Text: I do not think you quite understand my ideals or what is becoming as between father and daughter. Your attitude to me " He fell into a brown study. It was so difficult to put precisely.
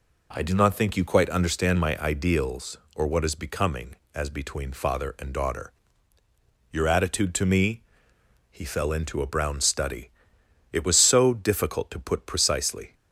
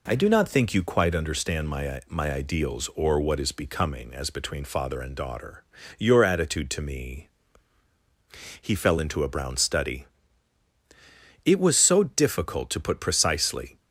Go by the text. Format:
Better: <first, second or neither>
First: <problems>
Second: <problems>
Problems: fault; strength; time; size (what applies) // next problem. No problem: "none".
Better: first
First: none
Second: says "my" twice; at 2.0 s